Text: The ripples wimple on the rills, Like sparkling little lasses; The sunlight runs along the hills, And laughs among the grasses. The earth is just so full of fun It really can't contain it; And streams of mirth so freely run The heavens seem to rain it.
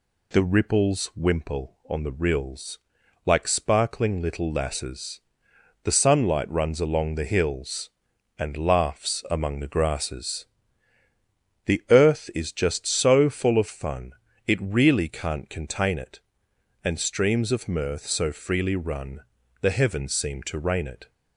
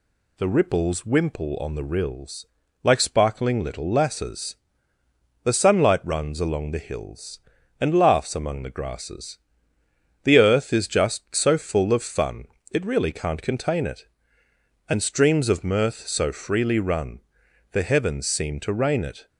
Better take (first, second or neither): neither